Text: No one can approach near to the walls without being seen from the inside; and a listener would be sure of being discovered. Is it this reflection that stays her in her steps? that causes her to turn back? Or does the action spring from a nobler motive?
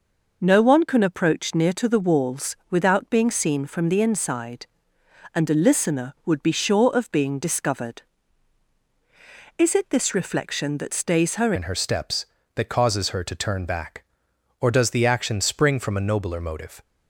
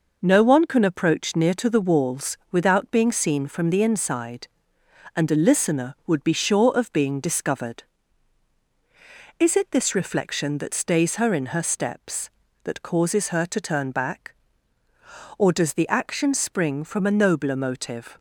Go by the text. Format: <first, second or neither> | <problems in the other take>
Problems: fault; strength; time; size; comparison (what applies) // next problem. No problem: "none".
second | changes voice at "in"; from 11.5 s on; 5.3 s long